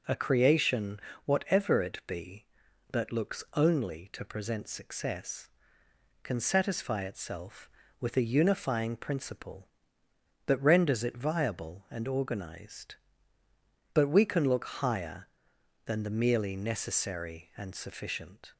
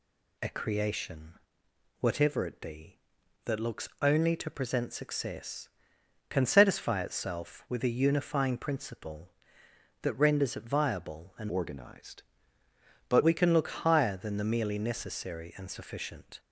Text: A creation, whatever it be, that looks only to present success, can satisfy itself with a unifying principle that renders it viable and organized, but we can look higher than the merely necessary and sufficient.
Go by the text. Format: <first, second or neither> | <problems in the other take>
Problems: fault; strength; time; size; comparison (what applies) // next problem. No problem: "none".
first | changes voice from "organized" to "but"; from 11.4 to 13.2 s; 1.8 s long